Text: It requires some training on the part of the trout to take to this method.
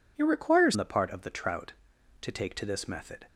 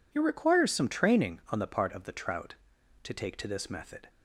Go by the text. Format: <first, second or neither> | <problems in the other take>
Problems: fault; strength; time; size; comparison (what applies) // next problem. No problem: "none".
second | skips "some training on"; at 0.7 s